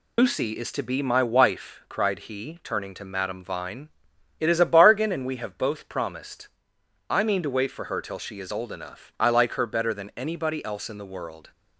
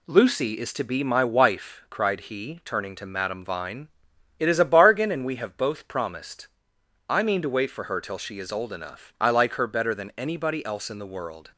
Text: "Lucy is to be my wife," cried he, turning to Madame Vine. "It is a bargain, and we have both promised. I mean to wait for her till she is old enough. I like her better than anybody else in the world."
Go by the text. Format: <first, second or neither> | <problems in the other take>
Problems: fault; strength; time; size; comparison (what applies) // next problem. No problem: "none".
second | loses the start of "Lucy"; at 0.1 s; 125 ms